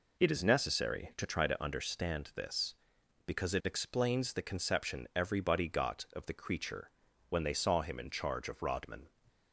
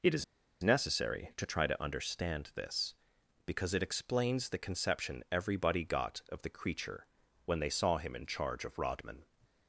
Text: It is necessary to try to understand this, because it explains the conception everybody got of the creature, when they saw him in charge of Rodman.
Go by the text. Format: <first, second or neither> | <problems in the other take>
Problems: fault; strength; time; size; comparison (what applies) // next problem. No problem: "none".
first | pauses between "is" and "necessary"; at 0.2 s; 0.38 s long